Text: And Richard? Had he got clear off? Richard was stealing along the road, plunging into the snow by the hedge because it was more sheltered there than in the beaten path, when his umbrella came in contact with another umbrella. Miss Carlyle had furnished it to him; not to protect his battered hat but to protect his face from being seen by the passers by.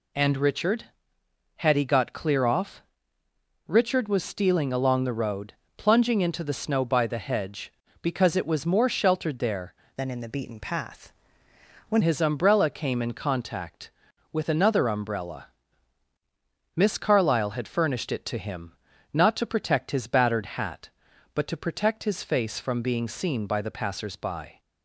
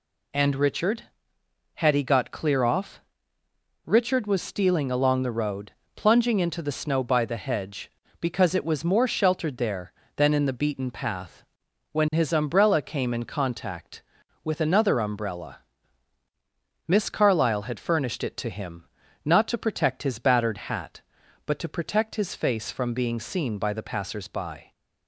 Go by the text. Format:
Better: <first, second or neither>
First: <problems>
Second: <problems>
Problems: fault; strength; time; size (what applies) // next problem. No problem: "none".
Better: second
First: changes voice from "than" to "when"; from 9.9 to 12.0 s; 2.1 s long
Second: none